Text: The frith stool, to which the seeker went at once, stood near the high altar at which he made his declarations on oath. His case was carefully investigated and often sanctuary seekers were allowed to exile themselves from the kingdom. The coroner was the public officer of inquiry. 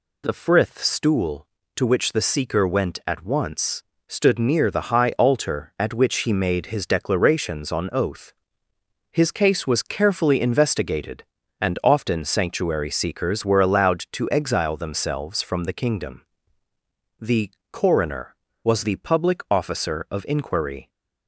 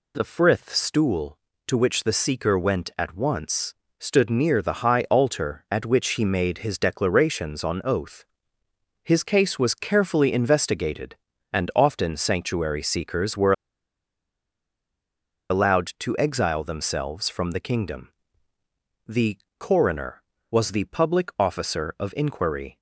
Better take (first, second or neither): first